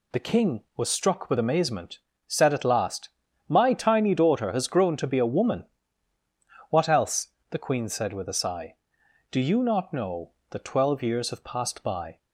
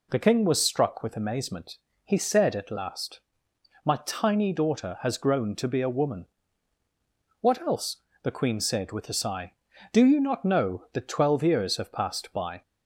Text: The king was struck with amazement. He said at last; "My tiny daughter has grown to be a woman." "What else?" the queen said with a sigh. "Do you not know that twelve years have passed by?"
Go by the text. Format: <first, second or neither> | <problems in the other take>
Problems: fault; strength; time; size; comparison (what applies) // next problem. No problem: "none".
second | skips "He"; at 2.1 s